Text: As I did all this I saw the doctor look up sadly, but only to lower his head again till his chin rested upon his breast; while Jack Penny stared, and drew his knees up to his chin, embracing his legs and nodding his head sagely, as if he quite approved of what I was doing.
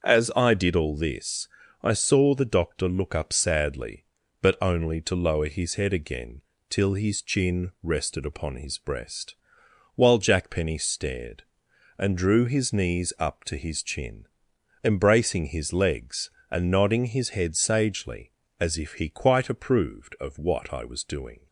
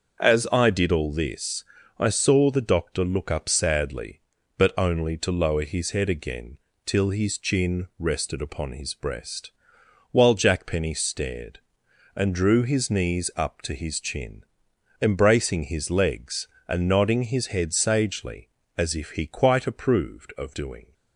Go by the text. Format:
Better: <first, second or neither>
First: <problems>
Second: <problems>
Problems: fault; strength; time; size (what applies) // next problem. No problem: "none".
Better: first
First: starts louder than the rest; until 1.1 s; 6.5 dB // pauses between "this" and "I"; slight; at 1.4 s; 0.34 s long // pauses between "again" and "till"; slight; at 6.4 s; 0.26 s long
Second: starts louder than the rest; until 1.2 s; 6.5 dB // pauses between "this" and "I"; slight; at 1.6 s; 0.34 s long // pauses between "again" and "till"; slight; at 6.5 s; 0.26 s long // skips "what I was"; at 20.5 s